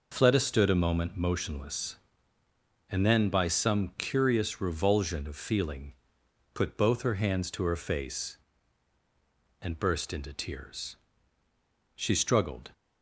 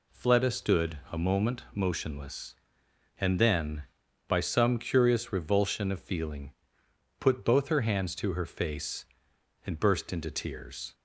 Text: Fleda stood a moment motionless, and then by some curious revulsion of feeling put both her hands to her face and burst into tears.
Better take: second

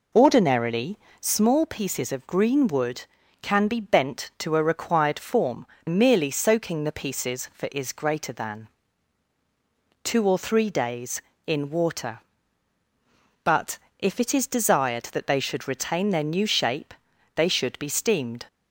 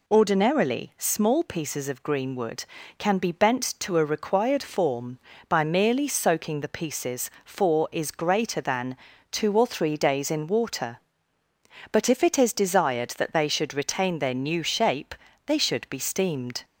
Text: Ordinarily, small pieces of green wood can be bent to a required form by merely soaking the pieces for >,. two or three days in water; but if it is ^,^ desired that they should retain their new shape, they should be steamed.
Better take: second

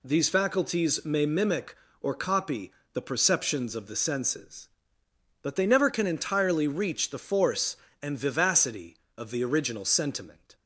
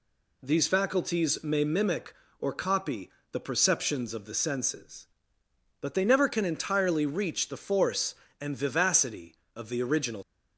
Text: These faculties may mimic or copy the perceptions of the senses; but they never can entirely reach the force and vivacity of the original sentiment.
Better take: first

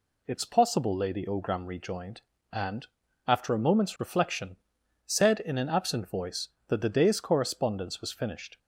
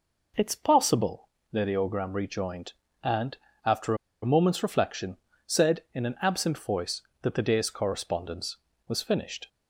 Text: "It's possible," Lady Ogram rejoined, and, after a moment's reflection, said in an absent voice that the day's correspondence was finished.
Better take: first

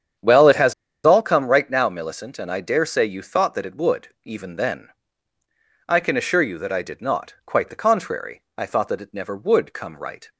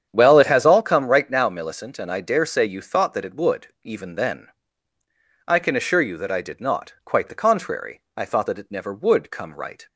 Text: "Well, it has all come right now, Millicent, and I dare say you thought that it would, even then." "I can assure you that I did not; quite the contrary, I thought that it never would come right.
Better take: second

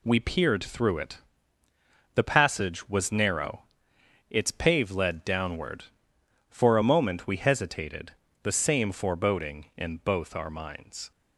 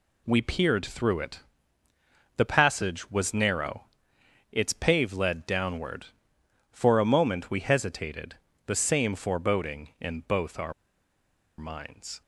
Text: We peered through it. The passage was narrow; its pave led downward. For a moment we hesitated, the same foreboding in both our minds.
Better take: first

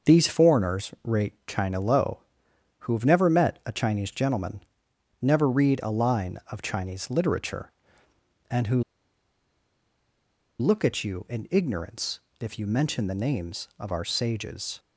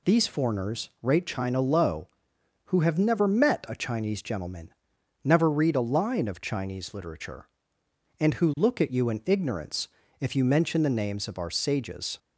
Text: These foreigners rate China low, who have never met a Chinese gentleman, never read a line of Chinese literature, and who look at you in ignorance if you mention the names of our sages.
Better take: second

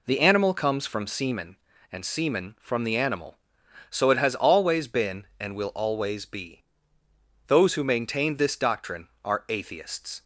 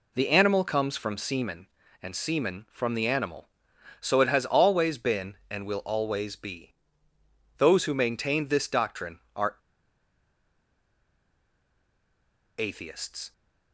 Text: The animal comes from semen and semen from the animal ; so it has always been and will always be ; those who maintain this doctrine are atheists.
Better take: first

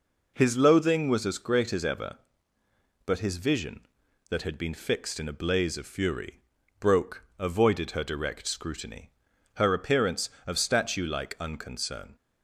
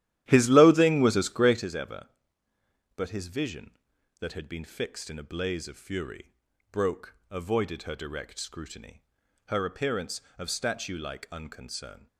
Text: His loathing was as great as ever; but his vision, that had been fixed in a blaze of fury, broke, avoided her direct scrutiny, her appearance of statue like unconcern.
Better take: first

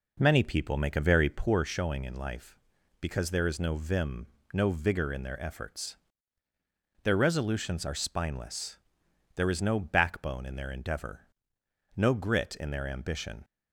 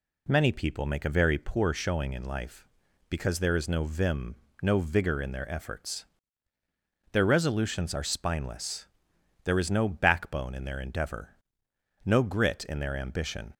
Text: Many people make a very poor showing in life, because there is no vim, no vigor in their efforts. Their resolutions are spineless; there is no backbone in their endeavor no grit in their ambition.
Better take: second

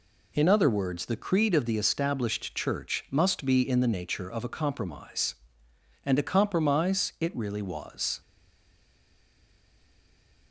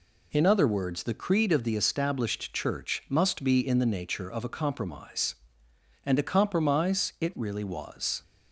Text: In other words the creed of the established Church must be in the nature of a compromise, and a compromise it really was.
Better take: second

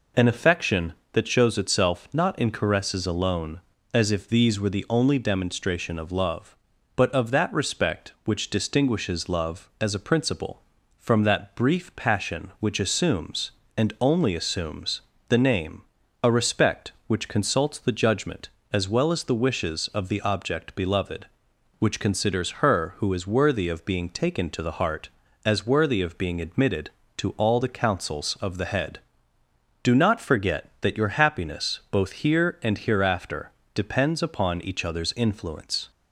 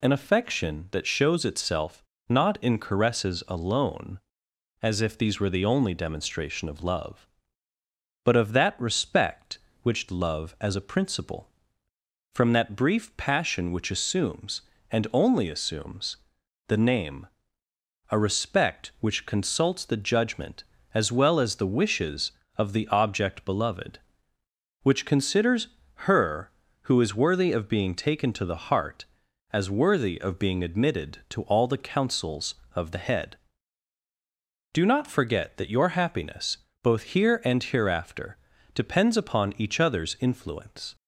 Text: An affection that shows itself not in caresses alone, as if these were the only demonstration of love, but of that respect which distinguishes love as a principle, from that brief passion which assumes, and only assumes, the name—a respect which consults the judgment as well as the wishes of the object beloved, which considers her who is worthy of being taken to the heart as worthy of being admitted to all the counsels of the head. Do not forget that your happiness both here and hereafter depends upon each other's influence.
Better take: first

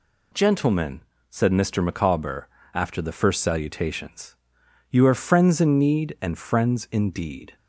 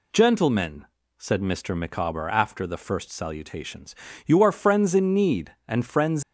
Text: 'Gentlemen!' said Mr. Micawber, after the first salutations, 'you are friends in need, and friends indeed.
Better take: first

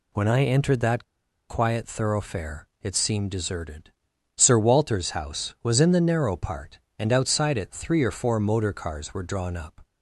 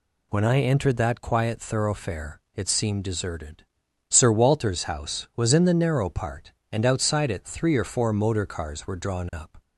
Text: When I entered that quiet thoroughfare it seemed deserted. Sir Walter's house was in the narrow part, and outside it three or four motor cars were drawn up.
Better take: second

